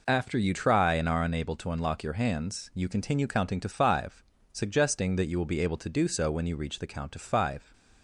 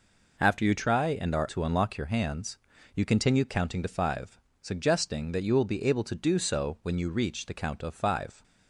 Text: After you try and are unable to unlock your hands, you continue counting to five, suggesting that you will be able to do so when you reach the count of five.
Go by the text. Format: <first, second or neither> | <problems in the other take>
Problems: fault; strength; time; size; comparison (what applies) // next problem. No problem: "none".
first | skips "unable"; at 1.4 s